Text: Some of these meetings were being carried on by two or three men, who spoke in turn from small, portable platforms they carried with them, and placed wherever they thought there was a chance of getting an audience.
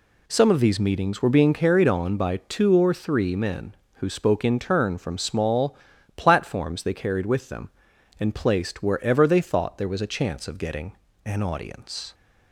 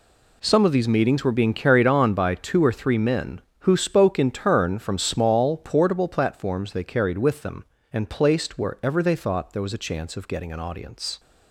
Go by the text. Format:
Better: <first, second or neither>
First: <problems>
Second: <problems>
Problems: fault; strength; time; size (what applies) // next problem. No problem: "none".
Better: second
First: skips "portable"; at 5.9 s // pauses between "getting" and "an"; slight; at 10.9 s; 0.32 s long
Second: none